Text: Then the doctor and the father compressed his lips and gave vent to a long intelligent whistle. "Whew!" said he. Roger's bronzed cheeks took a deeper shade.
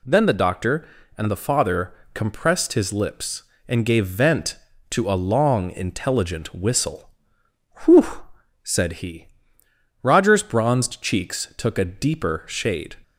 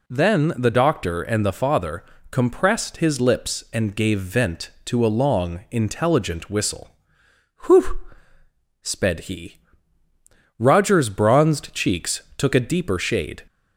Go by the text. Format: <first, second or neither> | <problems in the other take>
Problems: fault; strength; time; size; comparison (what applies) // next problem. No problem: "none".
first | pauses between "father" and "compressed"; slight; at 2.0 s; 0.26 s long; slight in the first // says "sped" for "said"; at 8.8 s // pauses between "cheeks" and "took"; slight; at 12.2 s; 0.16 s long